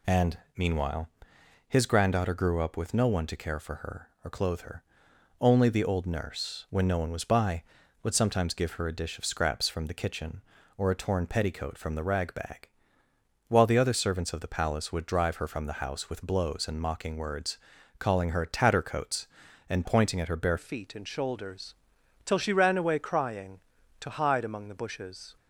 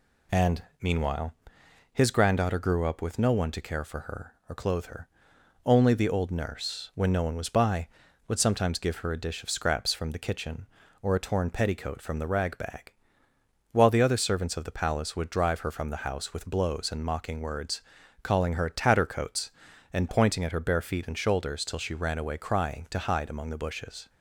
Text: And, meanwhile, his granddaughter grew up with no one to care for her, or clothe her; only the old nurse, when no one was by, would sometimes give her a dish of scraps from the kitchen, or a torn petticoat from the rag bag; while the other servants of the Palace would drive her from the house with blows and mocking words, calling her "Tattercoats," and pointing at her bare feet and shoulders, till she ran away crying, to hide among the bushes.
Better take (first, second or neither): second